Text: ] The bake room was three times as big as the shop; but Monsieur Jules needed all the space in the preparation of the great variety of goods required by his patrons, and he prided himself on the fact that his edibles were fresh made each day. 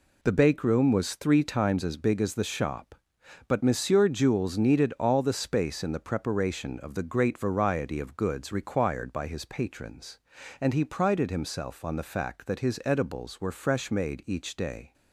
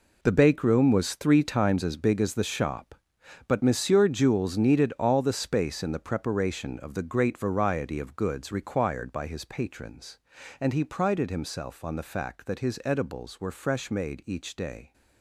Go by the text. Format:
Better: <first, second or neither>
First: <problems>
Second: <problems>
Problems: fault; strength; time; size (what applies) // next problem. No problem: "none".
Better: first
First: none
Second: gets quieter; strong; throughout; 12.5 dB